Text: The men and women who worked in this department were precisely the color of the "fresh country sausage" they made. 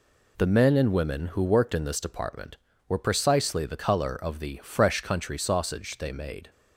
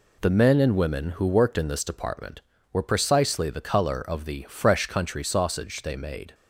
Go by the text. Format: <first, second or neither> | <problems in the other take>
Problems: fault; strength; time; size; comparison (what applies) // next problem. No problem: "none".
neither | none